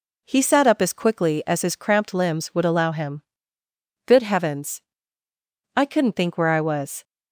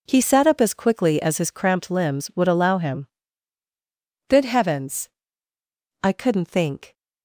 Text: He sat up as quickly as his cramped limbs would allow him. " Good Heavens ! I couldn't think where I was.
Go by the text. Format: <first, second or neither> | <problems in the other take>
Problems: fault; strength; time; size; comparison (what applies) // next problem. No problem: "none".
first | stops before "where I was"; at 6.9 s